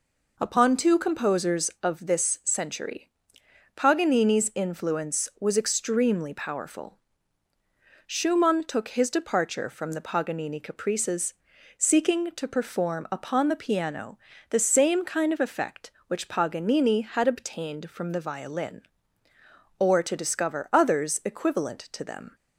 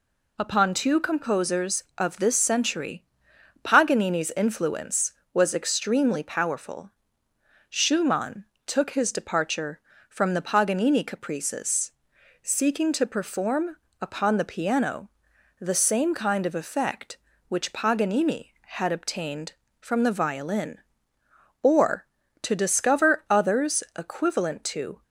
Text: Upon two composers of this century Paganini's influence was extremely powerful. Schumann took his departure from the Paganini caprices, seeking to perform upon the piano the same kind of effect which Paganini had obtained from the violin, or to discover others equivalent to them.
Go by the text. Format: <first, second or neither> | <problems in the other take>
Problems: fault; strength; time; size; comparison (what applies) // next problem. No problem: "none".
first | pauses between "century" and "Paganini's"; noticeable; at 3.0 s; 0.58 s long; noticeable in the first // pauses between "Schumann" and "took"; slight; at 8.4 s; 0.20 s long // pauses between "perform" and "upon"; slight; at 13.7 s; 0.24 s long // pauses between "piano" and "the"; noticeable; at 15.1 s; 0.50 s long; slight in the first // stops before "them"; at 25.0 s